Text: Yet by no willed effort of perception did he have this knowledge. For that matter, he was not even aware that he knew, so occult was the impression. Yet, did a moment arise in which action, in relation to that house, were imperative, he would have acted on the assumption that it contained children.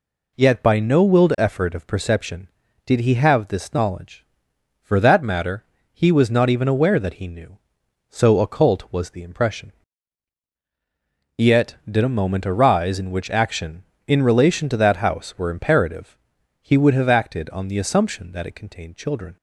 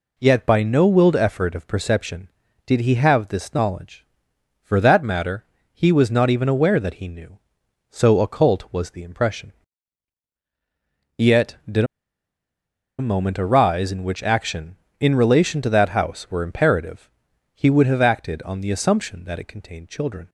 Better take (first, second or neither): first